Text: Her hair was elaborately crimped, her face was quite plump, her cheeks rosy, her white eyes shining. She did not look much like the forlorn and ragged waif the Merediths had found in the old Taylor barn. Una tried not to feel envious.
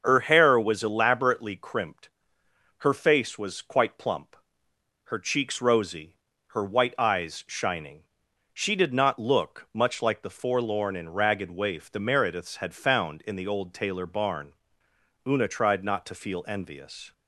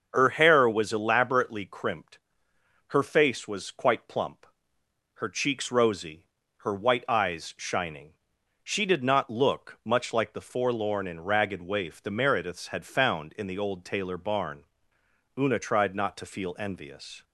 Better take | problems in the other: neither | starts louder than the rest; the same in both

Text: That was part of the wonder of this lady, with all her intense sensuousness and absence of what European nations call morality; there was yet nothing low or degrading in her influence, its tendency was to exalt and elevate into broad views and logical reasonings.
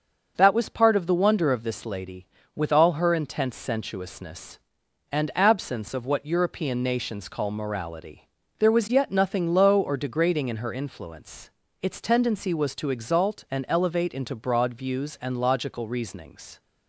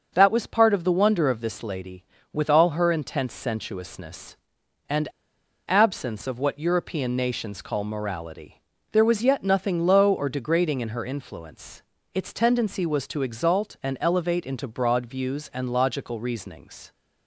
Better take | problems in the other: first | starts louder than the rest; until 1.1 s; 6.5 dB; also in the first // pauses between "and" and "absence"; noticeable; at 5.0 s; 0.58 s long

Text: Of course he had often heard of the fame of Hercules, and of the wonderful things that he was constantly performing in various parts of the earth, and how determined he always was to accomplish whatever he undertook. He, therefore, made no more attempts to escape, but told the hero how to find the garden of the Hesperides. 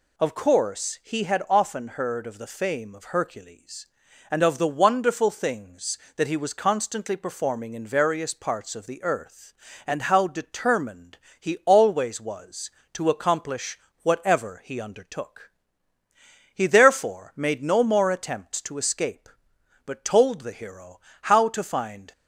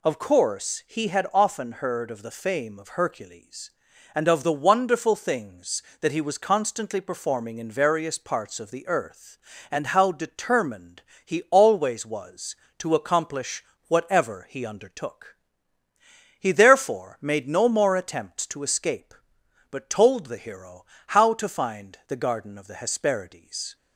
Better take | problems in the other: second | pauses between "determined" and "he"; slight; at 11.1 s; 0.23 s long; slight in the second // pauses between "accomplish" and "whatever"; slight; at 13.7 s; 0.26 s long; slight in the second // pauses between "hero" and "how"; slight; at 20.9 s; 0.22 s long; slight in the second // stops before "the garden of the Hesperides"; at 22.1 s

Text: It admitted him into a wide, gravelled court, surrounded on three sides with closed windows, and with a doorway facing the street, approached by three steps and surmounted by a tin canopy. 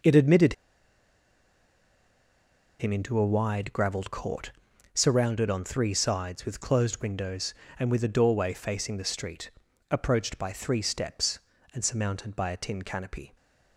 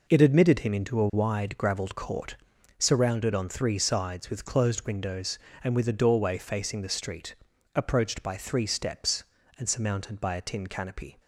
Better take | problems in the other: second | pauses between "admitted" and "him"; strong; at 0.5 s; 2.2 s long

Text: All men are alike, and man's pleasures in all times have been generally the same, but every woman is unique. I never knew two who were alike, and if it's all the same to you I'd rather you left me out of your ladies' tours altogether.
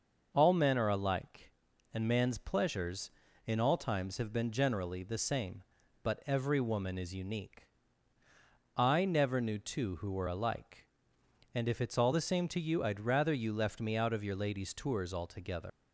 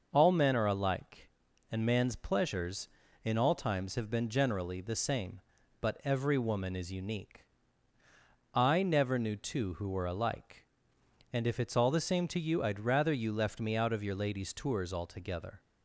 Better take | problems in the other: second | leaves "altogether" unfinished; at 15.6 s; 105 ms

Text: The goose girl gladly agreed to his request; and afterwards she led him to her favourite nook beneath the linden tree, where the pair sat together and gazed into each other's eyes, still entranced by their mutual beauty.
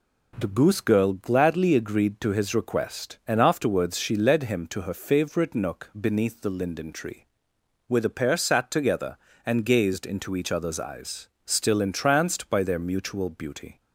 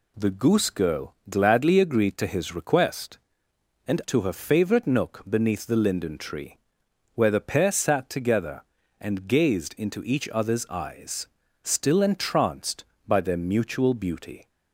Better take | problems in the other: first | skips "afterwards she led him"; at 4.0 s

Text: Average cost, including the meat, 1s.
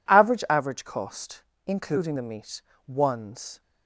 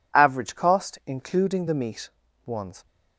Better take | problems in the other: second | says "Average" twice; at 0.4 s

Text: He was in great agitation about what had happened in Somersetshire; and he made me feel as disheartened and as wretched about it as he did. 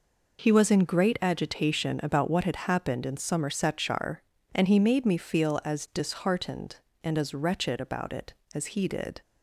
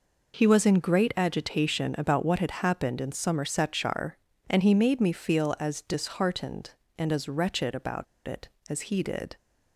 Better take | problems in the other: first | pauses between "about" and "it"; slight; at 8.0 s; 0.20 s long

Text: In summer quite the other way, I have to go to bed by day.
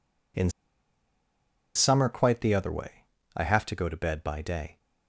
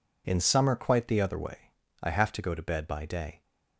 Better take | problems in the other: second | pauses between "In" and "summer"; strong; at 0.4 s; 1.2 s long

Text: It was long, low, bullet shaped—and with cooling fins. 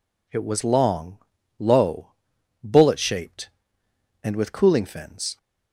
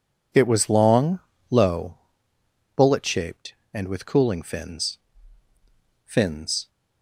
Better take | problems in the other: first | says "fins" twice; at 6.0 s

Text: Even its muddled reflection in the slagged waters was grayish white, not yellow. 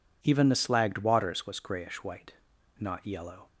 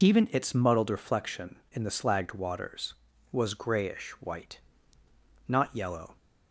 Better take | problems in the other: second | skips "its muddled reflection in"; at 0.4 s

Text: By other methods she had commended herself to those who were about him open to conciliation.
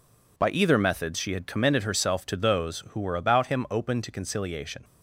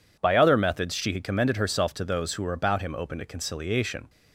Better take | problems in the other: second | says "either" for "other"; at 0.4 s

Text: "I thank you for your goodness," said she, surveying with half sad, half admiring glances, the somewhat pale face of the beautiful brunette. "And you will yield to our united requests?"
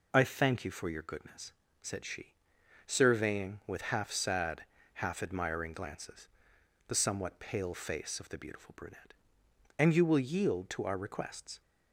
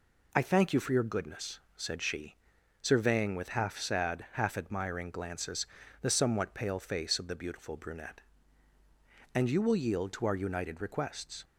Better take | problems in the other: second | skips "united"; at 10.9 s

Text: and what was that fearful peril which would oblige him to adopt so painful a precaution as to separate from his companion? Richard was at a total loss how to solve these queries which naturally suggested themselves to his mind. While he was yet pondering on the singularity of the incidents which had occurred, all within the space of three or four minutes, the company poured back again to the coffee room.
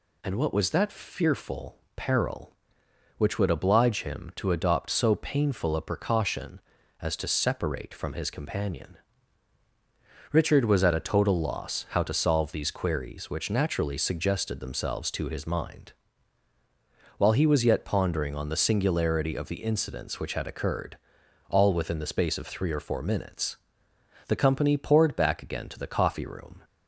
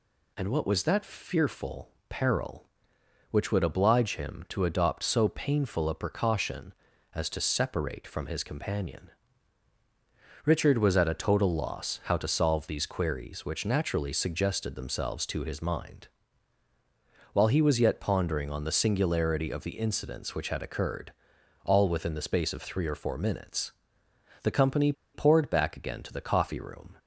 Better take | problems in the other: first | pauses between "fearful" and "peril"; slight; at 1.9 s; 0.18 s long; slight in the first // pauses between "company" and "poured"; slight; at 24.9 s; 0.21 s long

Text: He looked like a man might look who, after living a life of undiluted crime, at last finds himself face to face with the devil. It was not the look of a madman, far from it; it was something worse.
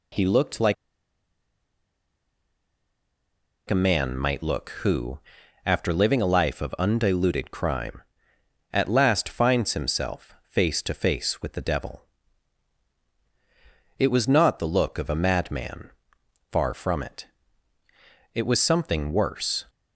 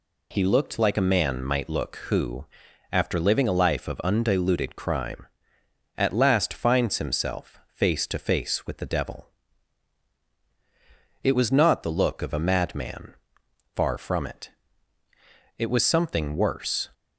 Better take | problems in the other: second | pauses between "like" and "a"; strong; at 0.7 s; 2.9 s long

